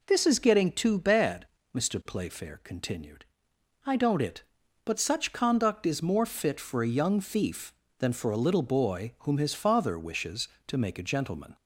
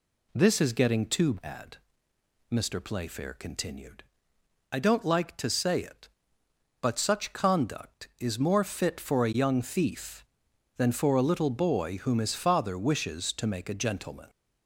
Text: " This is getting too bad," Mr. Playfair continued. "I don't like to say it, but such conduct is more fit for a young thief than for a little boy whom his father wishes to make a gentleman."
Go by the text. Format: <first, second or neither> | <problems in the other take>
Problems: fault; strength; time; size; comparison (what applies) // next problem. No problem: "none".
second | skips "like to say"; at 4.2 s